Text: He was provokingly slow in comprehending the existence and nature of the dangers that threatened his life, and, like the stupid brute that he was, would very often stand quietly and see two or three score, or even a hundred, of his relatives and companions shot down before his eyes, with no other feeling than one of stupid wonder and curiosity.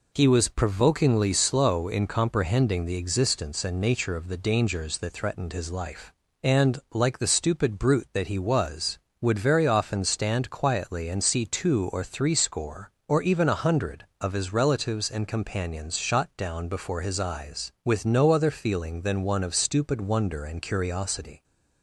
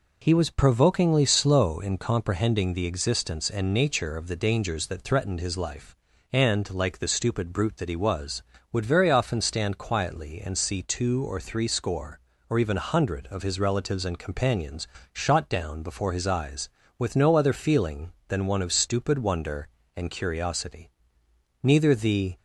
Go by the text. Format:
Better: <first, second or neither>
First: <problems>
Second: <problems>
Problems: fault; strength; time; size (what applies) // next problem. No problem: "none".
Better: first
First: none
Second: pauses between "companions" and "shot"; slight; at 14.8 s; 0.26 s long // goes on to say "Neither the"; noticeable; from 21.6 s on; 0.72 s long